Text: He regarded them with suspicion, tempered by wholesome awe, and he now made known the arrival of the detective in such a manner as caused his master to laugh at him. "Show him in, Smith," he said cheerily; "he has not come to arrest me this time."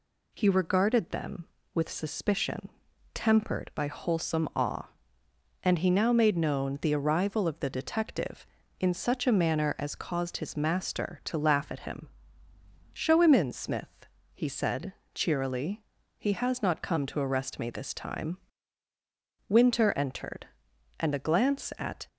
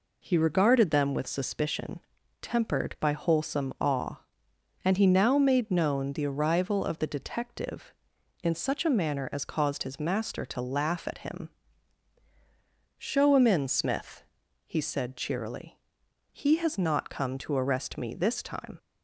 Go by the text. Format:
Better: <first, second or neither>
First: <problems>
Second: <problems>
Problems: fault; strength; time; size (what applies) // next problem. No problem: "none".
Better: second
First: pauses between "said" and "cheerily"; slight; at 14.9 s; 0.20 s long // goes on to say "Winter entered and a glance at"; strong; from 19.4 s on; 2.6 s long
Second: none